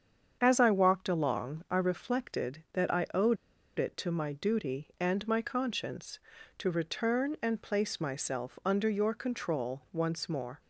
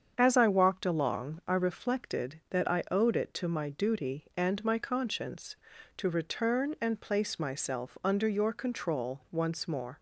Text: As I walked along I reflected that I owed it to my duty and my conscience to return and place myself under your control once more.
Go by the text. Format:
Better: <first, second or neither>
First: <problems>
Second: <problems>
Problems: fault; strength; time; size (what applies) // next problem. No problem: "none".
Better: second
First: starts louder than the rest; strong; until 1.4 s; 7.5 dB // pauses between "owed" and "it"; at 3.3 s; 0.41 s long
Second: starts louder than the rest; strong; until 1.1 s; 7.5 dB